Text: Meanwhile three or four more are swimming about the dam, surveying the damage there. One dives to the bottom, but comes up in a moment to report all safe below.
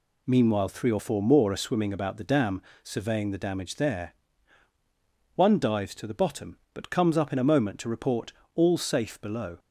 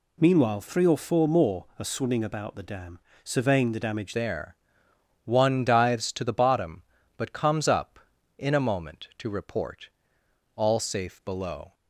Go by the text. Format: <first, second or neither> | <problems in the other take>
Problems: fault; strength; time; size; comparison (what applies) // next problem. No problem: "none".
first | changes voice at "there"; from 4.1 s on; 7.6 s long // pauses between "report" and "all"; noticeable; at 9.8 s; 0.68 s long; slight in the first